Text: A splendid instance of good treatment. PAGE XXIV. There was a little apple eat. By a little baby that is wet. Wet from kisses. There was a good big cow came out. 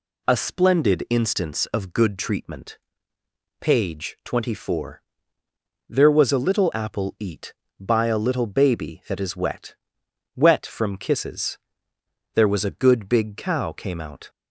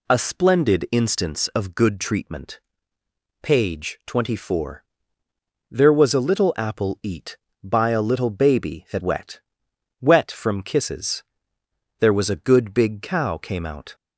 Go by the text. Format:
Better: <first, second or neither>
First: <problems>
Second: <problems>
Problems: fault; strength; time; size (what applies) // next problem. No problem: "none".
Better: first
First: none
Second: skips "is"; at 9.0 s